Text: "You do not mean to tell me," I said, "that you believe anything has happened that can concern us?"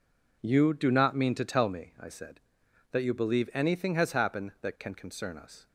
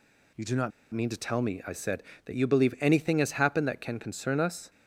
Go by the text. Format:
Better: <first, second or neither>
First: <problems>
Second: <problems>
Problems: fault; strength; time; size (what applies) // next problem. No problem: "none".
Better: first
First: none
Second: pauses between "not" and "mean"; slight; at 0.7 s; 0.23 s long